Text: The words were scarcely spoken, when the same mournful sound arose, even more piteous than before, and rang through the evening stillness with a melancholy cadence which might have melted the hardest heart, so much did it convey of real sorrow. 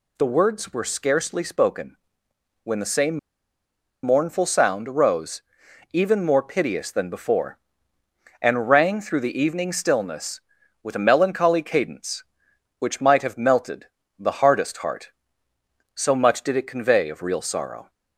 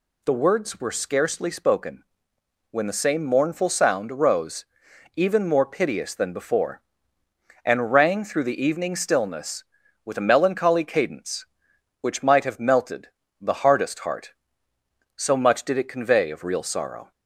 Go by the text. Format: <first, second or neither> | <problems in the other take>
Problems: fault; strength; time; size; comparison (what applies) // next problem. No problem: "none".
second | pauses between "same" and "mournful"; noticeable; at 3.1 s; 0.85 s long // pauses between "melted" and "the"; slight; at 13.8 s; 0.32 s long; slight in the second